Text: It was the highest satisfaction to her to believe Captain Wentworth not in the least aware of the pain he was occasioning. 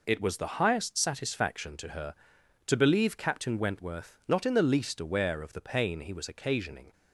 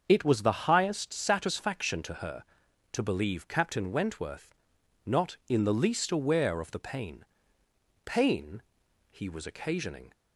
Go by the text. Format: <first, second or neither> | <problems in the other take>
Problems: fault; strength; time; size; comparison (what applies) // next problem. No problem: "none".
first | starts louder than the rest; until 1.0 s; 6.5 dB // pauses between "Wentworth" and "not"; noticeable; at 4.5 s; 0.52 s long // says "pain" twice; at 8.0 s